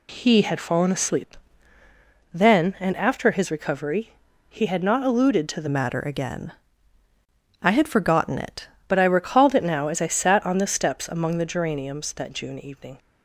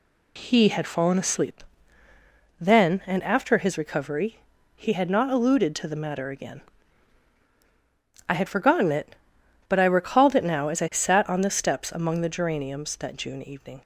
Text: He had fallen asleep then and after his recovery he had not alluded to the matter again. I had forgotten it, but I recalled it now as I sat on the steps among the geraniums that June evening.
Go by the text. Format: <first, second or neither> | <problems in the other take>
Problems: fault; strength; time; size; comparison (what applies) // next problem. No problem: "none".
second | pauses between "asleep" and "then"; noticeable; at 1.3 s; 0.98 s long; noticeable in the second // pauses between "recovery" and "he"; at 4.1 s; 0.38 s long; also in the second // changes voice from "matter" to "it"; from 5.6 to 8.6 s; 3.0 s long